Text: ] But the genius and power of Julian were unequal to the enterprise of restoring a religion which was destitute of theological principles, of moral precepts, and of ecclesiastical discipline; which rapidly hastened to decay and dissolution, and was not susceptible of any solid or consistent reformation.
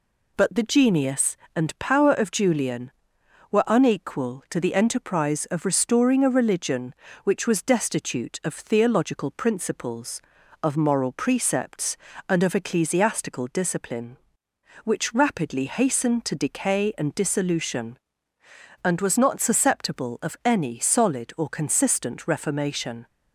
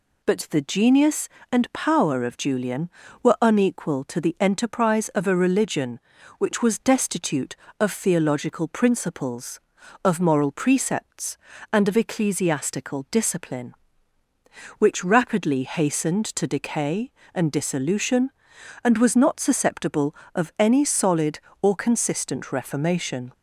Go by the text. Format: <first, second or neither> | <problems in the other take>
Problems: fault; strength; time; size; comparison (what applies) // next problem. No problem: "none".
first | skips "restoring"; at 5.2 s